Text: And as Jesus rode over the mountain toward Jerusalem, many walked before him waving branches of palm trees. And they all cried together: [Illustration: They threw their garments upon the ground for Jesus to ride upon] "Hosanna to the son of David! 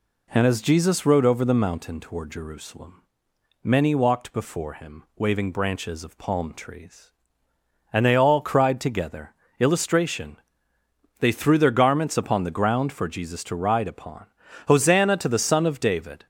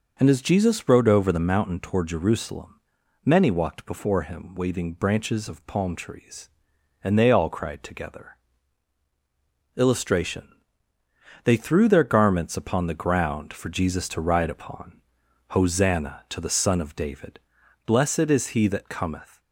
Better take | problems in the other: first | pauses between "upon" and "Hosanna"; noticeable; at 15.0 s; 0.46 s long; also in the first // goes on to say "Blessed is he that cometh"; from 17.8 s on; 1.5 s long

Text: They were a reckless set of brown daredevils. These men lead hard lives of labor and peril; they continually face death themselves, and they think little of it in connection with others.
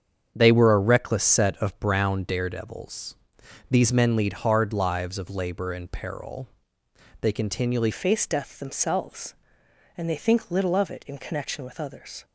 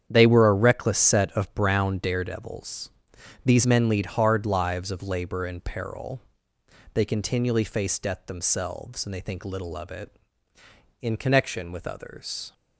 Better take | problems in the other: second | starts louder than the rest; strong; until 1.3 s; 7.5 dB; strong in the second // changes voice at "face"; from 7.9 s on; 4.3 s long

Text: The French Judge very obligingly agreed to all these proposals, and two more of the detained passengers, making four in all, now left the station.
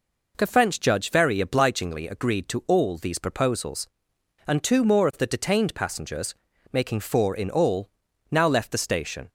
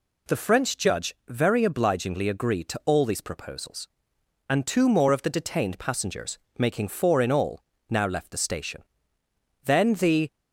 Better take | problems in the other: first | goes on to say "Then the"; noticeable; from 9.6 s on; 0.72 s long

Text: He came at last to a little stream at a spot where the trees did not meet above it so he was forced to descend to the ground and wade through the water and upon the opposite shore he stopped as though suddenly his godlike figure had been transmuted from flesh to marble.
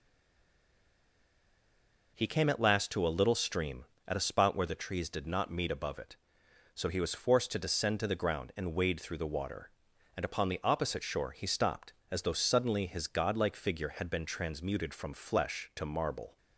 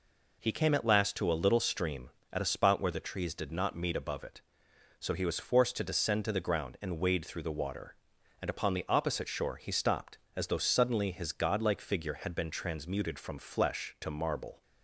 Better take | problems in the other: second | stays silent before the first word; until 2.1 s; 2.1 s long

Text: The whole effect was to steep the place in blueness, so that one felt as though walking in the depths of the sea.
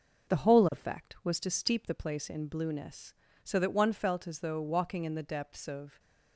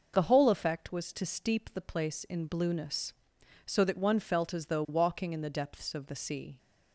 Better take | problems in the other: second | stops before "the sea"; at 5.9 s

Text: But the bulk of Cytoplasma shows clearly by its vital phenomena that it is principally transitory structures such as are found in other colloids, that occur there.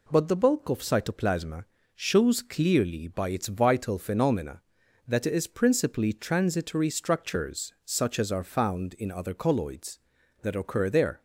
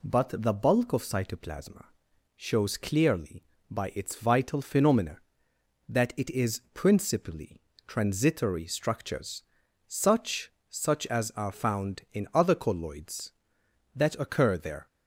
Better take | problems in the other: first | pauses between "Cytoplasma" and "shows"; noticeable; at 1.8 s; 0.52 s long; slight in the first // pauses between "principally" and "transitory"; slight; at 7.6 s; 0.26 s long // pauses between "structures" and "such"; at 9.4 s; 0.44 s long // says "such" twice; at 10.7 s

